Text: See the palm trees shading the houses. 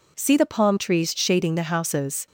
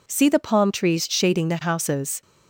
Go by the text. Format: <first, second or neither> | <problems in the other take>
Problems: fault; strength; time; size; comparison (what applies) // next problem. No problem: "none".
neither | none